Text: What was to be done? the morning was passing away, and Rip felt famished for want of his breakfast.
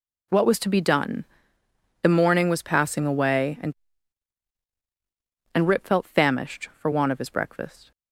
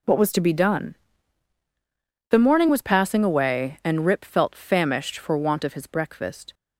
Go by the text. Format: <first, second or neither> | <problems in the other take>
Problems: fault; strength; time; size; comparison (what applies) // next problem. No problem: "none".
second | says "and" twice; at 5.5 s